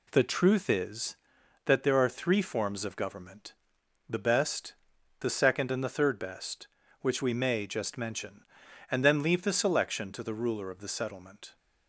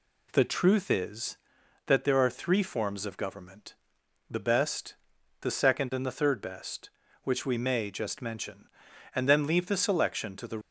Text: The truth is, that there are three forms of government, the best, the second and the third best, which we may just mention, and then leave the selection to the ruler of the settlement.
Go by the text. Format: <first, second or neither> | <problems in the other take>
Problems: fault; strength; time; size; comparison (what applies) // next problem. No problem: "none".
first | stops before "ruler of the settlement"; at 10.6 s